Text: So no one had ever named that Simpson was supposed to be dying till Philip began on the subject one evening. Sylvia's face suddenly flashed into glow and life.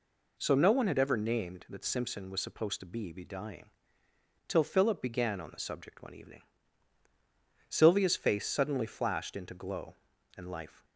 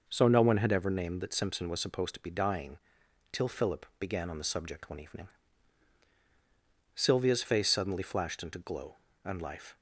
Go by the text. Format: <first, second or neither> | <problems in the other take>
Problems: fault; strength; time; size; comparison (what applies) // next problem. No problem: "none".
second | says "be" twice; at 3.1 s // pauses between "dying" and "till"; noticeable; at 3.6 s; 0.76 s long; noticeable in the second